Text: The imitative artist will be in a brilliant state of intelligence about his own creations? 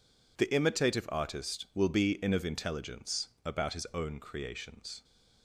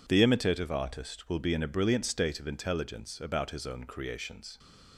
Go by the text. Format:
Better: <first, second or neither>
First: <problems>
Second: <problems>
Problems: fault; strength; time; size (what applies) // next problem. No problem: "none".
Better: second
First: skips "a brilliant state"; at 2.3 s // pauses between "intelligence" and "about"; slight; at 3.2 s; 0.18 s long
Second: none